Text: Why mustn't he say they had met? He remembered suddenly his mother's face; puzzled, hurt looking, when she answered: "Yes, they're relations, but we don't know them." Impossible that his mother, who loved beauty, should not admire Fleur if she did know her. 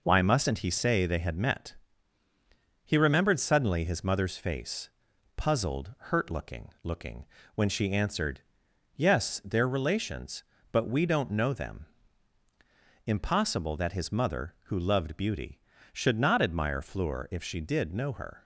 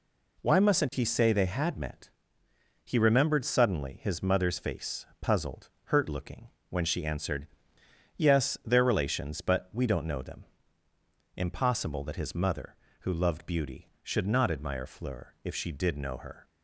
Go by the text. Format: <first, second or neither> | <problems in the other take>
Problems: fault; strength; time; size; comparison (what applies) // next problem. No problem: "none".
second | says "looking" twice; at 6.8 s